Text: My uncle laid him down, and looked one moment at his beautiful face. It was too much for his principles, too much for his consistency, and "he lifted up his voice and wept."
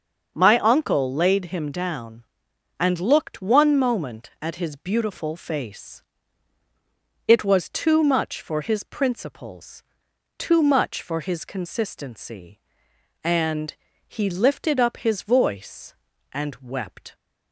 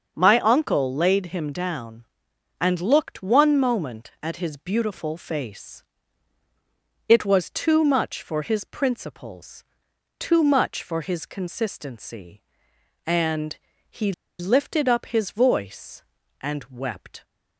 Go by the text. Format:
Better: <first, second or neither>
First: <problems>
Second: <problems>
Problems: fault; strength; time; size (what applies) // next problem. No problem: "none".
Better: first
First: starts louder than the rest; until 1.3 s; 6.5 dB // pauses between "and" and "he"; slight; at 13.7 s; 0.32 s long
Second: starts louder than the rest; until 1.1 s; 6.5 dB // pauses between "and" and "he"; slight; at 13.5 s; 0.32 s long // pauses between "he" and "lifted"; slight; at 14.1 s; 0.27 s long